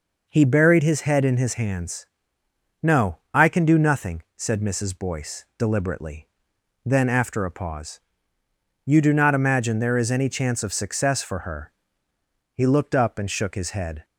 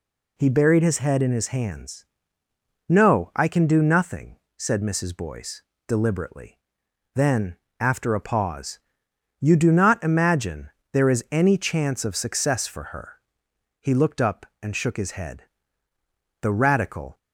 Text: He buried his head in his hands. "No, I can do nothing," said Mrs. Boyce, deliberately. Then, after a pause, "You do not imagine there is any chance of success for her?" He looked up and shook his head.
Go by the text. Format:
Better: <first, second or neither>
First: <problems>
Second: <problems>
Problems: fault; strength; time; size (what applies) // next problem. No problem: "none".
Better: first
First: none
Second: pauses between "imagine" and "there"; slight; at 10.6 s; 0.22 s long // goes on to say "The Radical"; noticeable; from 16.4 s on; 0.76 s long